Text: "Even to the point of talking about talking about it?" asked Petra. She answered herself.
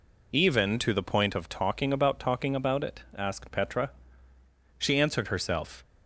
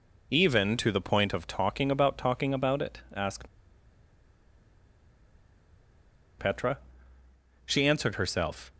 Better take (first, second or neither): first